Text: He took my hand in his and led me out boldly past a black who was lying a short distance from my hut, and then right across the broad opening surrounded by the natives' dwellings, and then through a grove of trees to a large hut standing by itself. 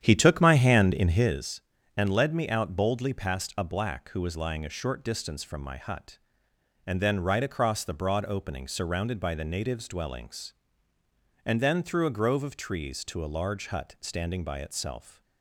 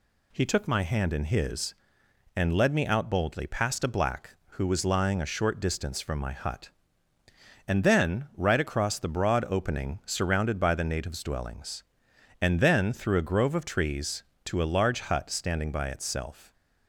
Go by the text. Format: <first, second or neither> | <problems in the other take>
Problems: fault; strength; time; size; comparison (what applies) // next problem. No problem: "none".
second | starts louder than the rest; strong; until 1.4 s; 10 dB